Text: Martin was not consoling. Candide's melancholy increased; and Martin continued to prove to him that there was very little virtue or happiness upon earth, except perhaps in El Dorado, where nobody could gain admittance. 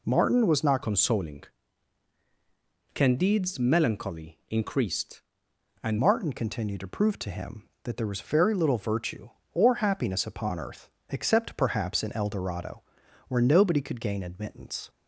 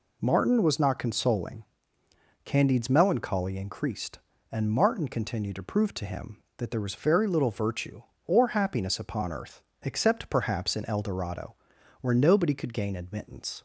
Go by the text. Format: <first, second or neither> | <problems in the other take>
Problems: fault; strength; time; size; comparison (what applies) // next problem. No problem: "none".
second | changes voice from "consoling" to "and"; from 0.8 to 5.9 s; 5.1 s long